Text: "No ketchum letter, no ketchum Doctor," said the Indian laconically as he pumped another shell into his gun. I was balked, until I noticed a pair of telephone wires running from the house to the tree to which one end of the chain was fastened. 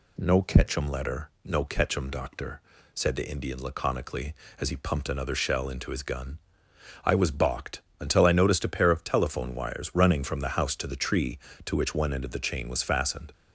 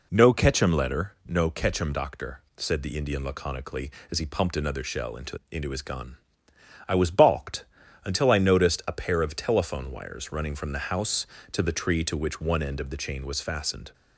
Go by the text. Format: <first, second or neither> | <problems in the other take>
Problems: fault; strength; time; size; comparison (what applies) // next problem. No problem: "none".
first | says "into" twice; at 5.5 s